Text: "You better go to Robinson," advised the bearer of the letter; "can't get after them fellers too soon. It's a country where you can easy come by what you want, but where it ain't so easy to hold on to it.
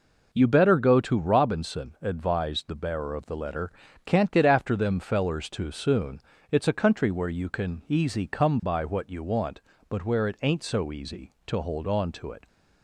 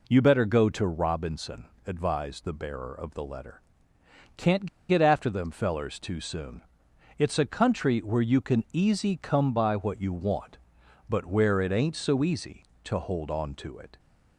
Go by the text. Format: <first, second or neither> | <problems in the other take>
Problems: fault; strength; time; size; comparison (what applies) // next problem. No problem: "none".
first | pauses between "can't" and "get"; slight; at 4.6 s; 0.22 s long